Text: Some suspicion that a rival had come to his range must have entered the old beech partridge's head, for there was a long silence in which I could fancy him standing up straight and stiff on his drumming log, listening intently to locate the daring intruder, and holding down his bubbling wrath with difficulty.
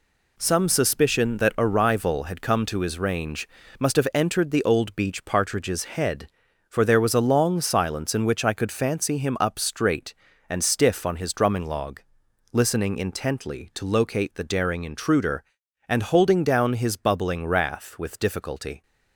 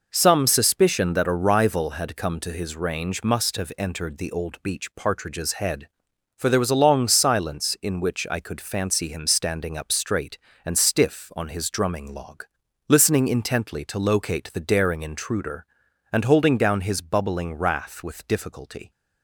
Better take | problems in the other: second | pauses between "range" and "must"; slight; at 3.4 s; 0.32 s long // skips "standing"; at 9.3 s

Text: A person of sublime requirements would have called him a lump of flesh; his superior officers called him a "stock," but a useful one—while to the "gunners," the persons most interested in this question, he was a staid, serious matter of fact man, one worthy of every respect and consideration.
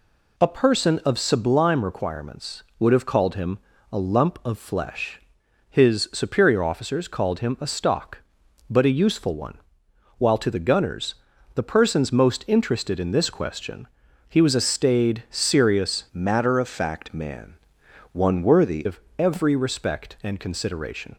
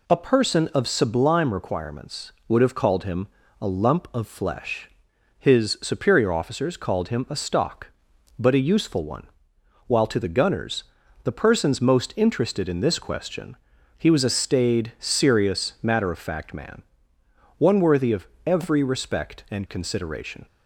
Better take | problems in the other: second | pauses between "him" and "a"; slight; at 3.5 s; 0.32 s long; slight in the second // changes voice from "matter" to "worthy"; from 16.1 to 18.8 s; 2.7 s long // pauses between "of" and "every"; slight; at 18.9 s; 0.18 s long; slight in the second

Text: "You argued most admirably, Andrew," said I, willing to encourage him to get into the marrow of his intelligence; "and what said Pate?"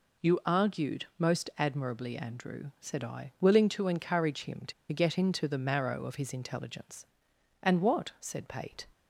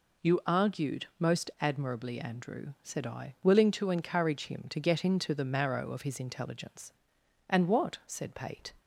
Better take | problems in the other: second | pauses between "to" and "get"; slight; at 4.7 s; 0.19 s long

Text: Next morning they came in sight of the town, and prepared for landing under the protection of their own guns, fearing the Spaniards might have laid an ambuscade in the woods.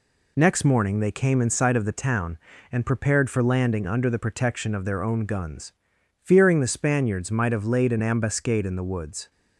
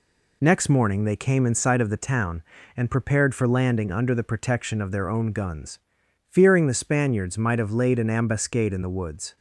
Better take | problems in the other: neither | none

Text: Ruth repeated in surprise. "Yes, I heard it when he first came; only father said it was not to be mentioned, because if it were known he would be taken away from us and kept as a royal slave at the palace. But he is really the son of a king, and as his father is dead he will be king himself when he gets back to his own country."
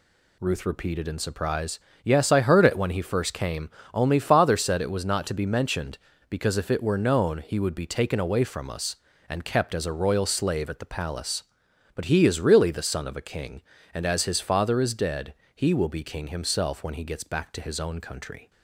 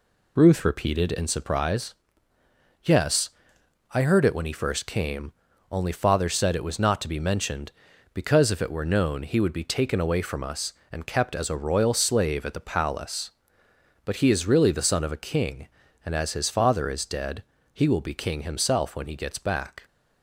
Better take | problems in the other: first | pauses between "dead" and "he"; slight; at 17.4 s; 0.30 s long; slight in the first // stops before "to his own country"; at 19.8 s

